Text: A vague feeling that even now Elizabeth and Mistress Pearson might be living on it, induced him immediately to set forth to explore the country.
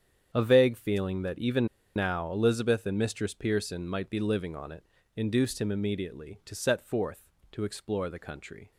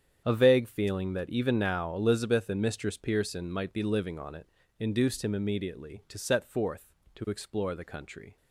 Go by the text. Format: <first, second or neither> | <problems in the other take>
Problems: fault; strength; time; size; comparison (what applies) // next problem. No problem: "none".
second | starts louder than the rest; strong; until 1.3 s; 8.5 dB; strong in the second // pauses between "even" and "now"; slight; at 1.6 s; 0.28 s long